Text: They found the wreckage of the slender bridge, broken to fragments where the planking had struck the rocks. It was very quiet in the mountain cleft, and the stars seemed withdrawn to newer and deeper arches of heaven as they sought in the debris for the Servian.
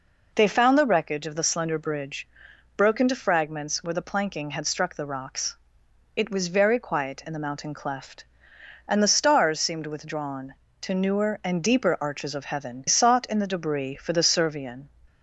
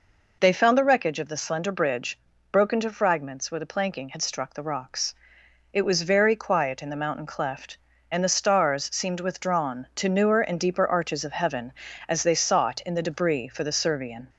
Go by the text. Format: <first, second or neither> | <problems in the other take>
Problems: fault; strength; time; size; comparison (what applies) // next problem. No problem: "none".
second | skips "as they"; at 12.8 s